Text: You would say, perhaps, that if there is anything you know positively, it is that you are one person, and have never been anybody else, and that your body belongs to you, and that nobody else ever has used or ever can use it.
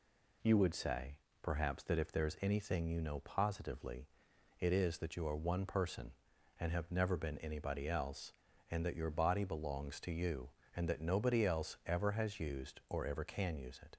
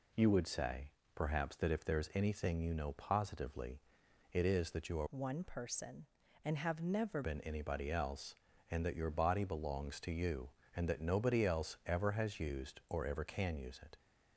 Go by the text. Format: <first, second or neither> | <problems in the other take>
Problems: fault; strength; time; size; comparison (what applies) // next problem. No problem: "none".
first | changes voice from "one" to "never"; from 5.0 to 7.2 s; 2.2 s long